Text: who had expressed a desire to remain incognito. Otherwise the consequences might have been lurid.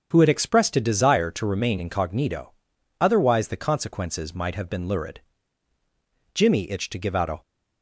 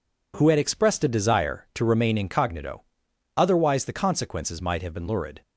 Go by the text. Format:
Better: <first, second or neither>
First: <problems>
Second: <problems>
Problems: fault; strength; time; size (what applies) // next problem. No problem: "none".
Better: second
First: starts louder than the rest; strong; until 1.1 s; 7.5 dB // goes on to say "Jimmy itched to give out a"; noticeable; from 6.3 s on; 1.0 s long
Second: none